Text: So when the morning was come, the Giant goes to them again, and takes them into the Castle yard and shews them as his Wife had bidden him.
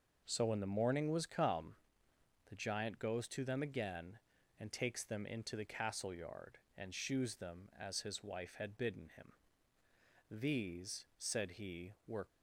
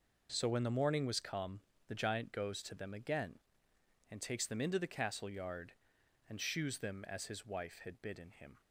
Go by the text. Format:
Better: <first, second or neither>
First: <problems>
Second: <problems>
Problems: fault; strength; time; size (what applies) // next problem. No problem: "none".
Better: second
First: goes on to say "These said he were"; strong; from 10.4 s on; 1.8 s long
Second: none